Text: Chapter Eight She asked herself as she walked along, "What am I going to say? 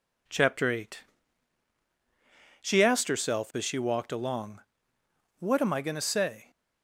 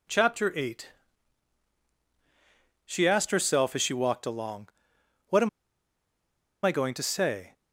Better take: first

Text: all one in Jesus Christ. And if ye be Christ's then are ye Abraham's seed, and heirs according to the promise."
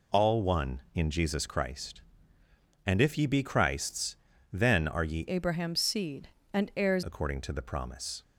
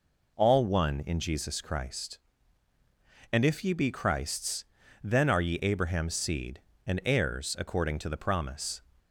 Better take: second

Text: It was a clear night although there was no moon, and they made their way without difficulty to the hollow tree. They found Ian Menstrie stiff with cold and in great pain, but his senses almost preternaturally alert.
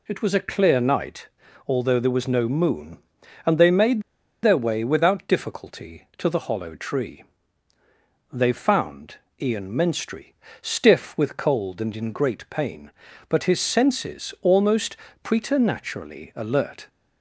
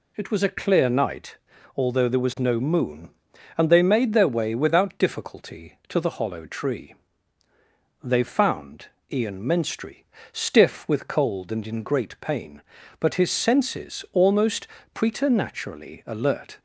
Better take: second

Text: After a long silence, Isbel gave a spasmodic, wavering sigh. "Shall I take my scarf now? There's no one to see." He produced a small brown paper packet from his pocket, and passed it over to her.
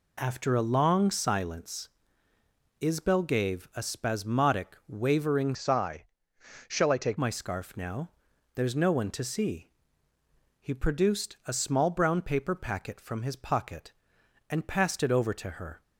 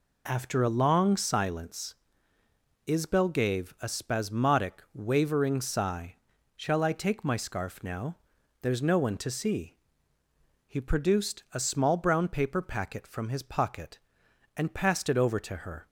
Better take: second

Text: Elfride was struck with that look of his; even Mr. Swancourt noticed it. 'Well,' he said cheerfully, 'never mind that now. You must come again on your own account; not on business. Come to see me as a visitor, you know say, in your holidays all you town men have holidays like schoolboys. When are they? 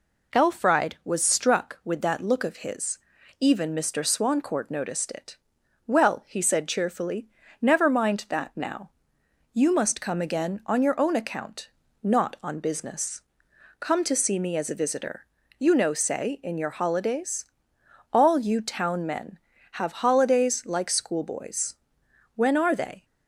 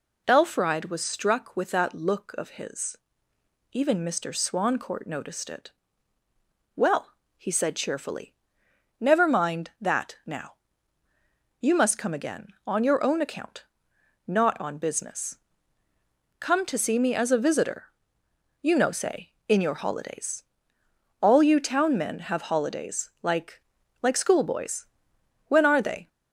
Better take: first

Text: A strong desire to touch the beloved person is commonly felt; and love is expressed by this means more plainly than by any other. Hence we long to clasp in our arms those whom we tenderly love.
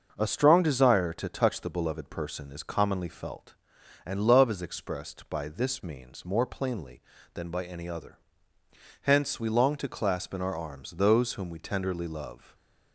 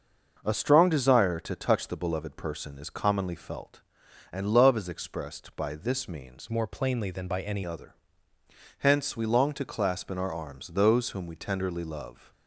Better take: first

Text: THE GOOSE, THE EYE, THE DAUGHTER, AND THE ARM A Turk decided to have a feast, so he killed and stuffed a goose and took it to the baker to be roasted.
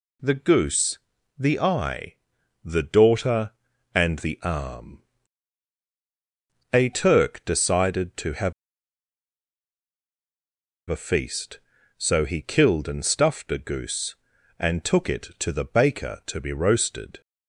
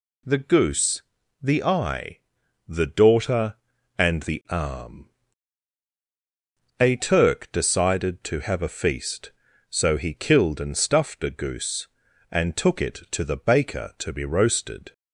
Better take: second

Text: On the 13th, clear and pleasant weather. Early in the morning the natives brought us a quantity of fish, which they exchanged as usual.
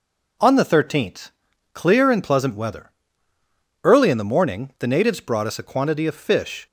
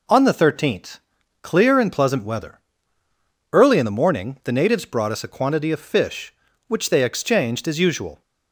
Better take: second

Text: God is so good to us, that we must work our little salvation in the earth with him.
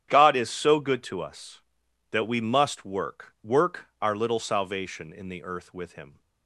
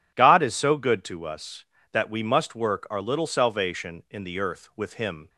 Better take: second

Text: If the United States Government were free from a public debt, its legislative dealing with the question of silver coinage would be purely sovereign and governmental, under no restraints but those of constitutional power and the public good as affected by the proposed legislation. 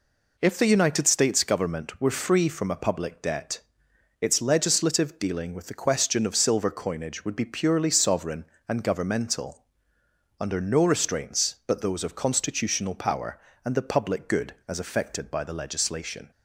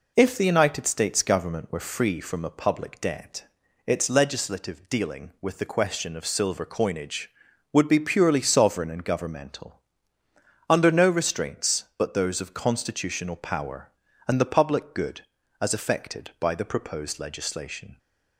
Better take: second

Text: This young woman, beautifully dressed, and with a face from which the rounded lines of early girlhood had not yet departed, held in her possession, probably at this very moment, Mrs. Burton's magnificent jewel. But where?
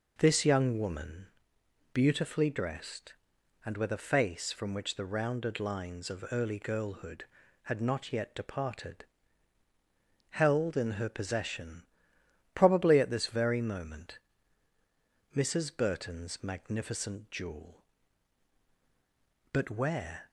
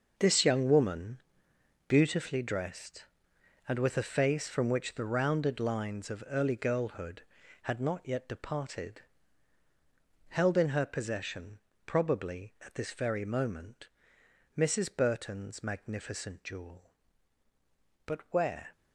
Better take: first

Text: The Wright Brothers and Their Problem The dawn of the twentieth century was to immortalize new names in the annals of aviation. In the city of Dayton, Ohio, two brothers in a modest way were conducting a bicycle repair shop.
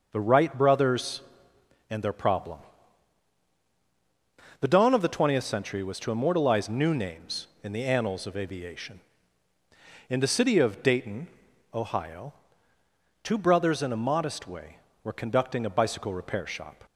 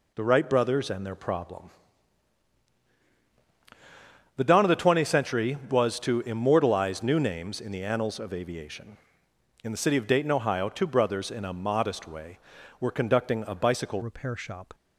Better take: first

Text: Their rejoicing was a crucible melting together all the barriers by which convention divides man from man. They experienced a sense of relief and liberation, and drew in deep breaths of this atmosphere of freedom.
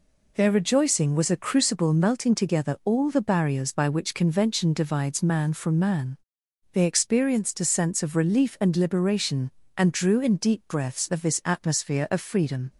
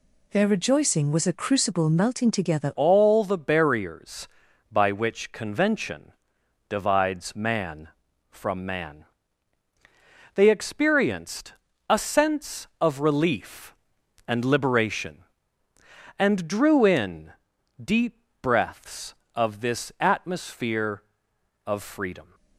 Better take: first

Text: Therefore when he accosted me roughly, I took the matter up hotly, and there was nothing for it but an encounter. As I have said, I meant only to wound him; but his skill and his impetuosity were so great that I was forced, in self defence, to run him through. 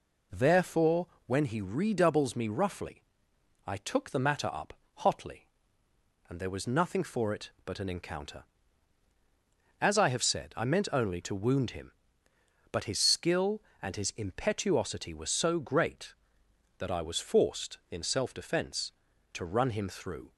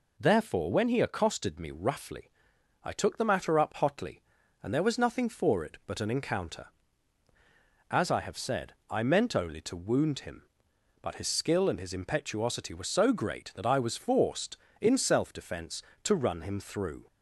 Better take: second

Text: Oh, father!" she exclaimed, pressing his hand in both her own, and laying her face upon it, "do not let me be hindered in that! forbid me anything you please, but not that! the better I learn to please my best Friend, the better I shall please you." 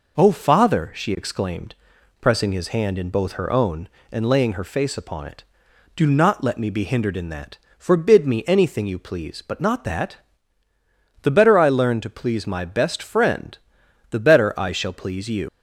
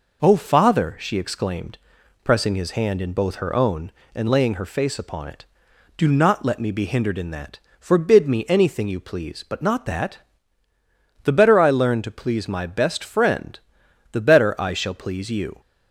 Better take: second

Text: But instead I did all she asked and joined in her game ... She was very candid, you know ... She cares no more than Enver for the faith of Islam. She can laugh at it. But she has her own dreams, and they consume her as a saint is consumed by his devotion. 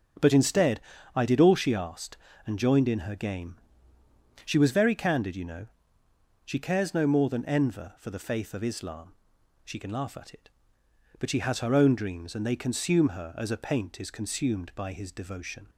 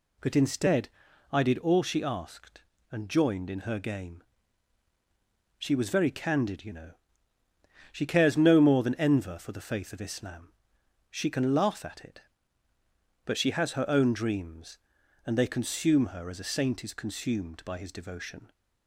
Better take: second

